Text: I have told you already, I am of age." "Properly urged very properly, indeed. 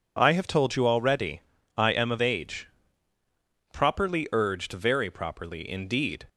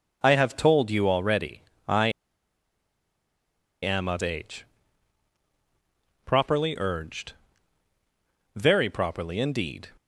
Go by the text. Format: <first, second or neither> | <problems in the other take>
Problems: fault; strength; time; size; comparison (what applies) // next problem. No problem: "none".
first | pauses between "I" and "am"; strong; at 2.0 s; 1.7 s long // pauses between "urged" and "very"; at 7.3 s; 1.2 s long